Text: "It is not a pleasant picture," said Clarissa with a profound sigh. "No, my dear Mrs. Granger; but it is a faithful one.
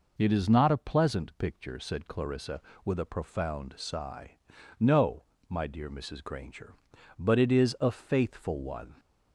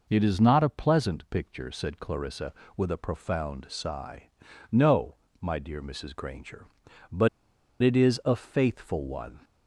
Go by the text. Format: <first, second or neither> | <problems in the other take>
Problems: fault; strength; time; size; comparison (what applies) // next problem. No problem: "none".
first | pauses between "but" and "it"; noticeable; at 7.2 s; 0.53 s long